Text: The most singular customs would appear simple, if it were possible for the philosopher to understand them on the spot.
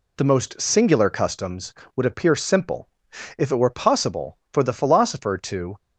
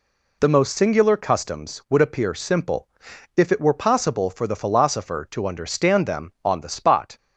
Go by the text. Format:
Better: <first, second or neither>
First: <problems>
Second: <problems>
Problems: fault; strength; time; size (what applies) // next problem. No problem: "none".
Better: second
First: stops before "understand them on the spot"; at 5.7 s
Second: none